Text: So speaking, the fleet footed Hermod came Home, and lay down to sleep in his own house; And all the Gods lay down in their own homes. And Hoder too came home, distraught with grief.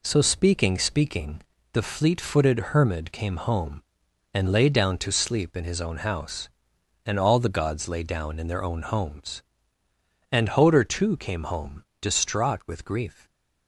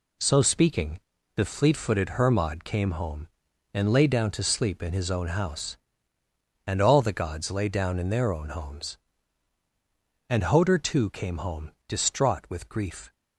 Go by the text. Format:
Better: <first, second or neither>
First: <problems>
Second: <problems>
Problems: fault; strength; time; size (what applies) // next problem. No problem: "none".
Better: second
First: says "speaking" twice; at 0.7 s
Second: none